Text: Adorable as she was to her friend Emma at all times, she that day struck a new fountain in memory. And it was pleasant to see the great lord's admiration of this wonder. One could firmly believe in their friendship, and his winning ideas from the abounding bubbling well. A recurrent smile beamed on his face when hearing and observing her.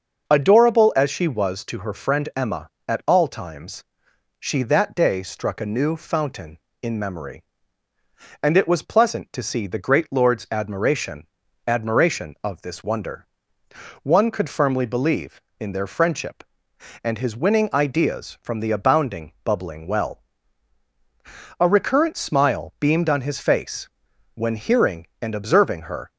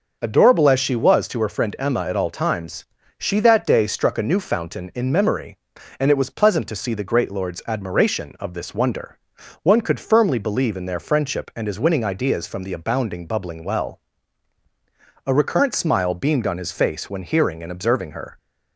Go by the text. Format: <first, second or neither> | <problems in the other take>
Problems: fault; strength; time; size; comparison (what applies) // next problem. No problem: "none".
second | starts louder than the rest; noticeable; until 1.3 s; 6 dB; noticeable in the second // says "admiration" twice; at 11.6 s // pauses between "face" and "when"; noticeable; at 23.8 s; 0.46 s long